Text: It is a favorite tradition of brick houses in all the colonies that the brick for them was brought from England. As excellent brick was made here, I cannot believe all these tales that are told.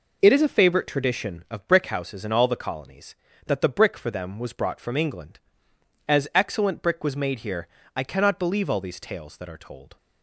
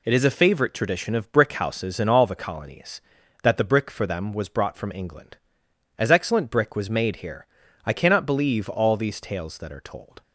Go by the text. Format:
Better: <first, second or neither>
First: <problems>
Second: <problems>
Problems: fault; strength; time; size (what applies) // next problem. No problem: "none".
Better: neither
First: none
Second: none